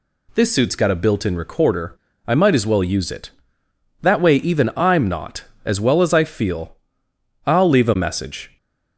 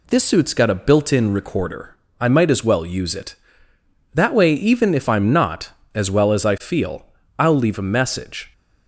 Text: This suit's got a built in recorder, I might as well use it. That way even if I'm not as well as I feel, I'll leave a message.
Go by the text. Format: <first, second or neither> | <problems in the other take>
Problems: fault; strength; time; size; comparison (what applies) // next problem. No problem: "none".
second | skips "if"; at 4.7 s